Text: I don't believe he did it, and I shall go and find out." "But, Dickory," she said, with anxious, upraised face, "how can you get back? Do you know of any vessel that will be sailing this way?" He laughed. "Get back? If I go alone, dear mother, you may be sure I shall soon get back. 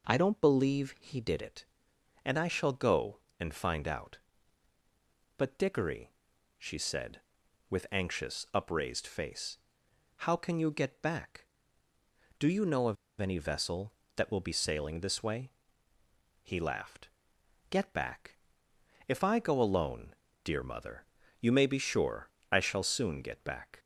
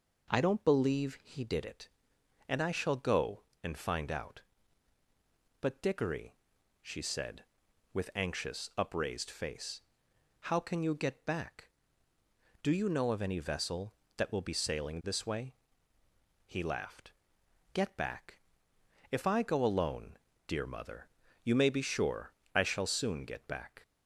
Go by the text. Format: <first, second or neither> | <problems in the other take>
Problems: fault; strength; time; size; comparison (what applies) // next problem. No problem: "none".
second | pauses between "of" and "any"; slight; at 12.9 s; 0.26 s long // pauses between "sure" and "I"; slight; at 22.2 s; 0.24 s long; slight in the second